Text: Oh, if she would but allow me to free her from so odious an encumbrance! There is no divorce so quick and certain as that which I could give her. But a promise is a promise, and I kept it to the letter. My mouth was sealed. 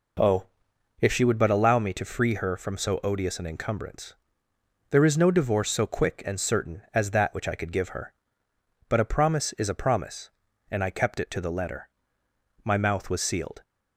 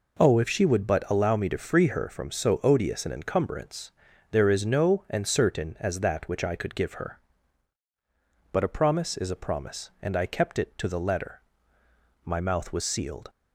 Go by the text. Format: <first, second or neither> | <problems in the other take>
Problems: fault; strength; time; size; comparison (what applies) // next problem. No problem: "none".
first | skips "divorce so quick"; at 5.0 s